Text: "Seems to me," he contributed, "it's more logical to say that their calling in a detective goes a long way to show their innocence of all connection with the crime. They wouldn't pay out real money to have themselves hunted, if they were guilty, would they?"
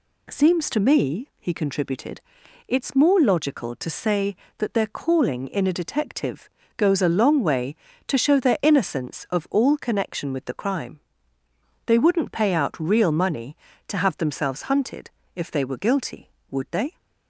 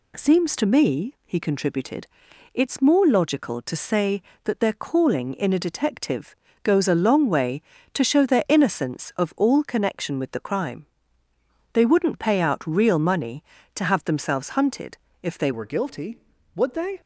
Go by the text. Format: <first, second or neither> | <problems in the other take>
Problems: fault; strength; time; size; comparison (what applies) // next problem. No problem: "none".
first | pauses between "detective" and "goes"; slight; at 6.3 s; 0.26 s long; slight in the first // changes voice at "were"; from 15.5 s on; 1.5 s long